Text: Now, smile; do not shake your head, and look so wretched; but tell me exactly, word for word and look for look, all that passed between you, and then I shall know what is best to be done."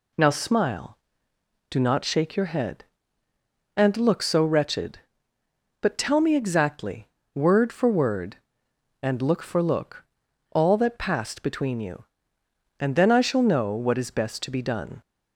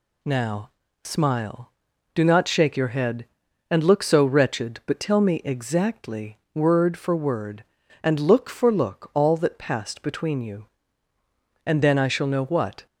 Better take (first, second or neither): first